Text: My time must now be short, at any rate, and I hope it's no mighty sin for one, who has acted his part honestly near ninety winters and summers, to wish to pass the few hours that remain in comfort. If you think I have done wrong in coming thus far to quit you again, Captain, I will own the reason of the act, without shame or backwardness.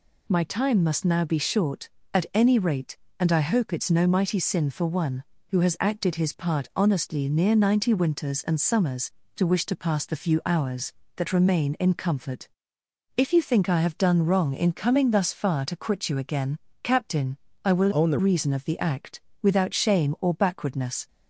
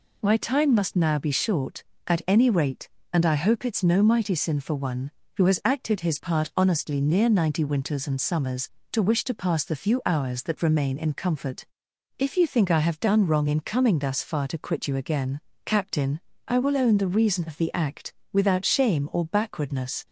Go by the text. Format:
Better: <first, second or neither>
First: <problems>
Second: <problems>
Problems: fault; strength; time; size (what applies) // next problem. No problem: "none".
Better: second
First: changes voice from "own" to "the"; from 17.9 to 18.1 s; 0.2 s long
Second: none